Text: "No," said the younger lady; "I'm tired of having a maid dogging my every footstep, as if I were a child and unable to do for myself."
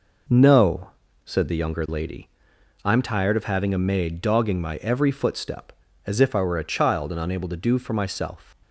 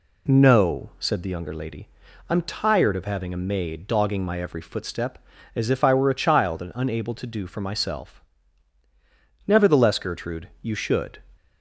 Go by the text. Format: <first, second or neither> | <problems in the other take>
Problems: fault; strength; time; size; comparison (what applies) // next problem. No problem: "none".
first | goes on to say "Nevertheless Gertrude you should"; strong; from 9.4 s on; 1.7 s long